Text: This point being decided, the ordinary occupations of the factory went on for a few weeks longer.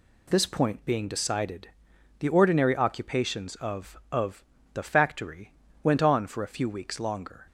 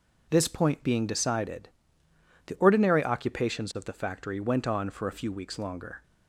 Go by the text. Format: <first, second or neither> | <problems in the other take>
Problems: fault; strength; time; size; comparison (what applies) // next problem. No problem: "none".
second | says "of" twice; at 4.1 s // pauses between "factory" and "went"; slight; at 5.5 s; 0.30 s long